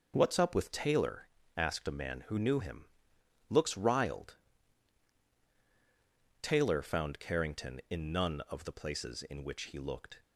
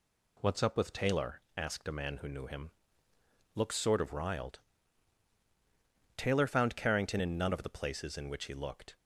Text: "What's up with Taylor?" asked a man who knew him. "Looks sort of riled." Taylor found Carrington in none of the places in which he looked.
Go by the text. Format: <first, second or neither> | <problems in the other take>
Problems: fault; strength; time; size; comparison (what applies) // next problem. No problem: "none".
second | skips "sort of"; at 3.7 s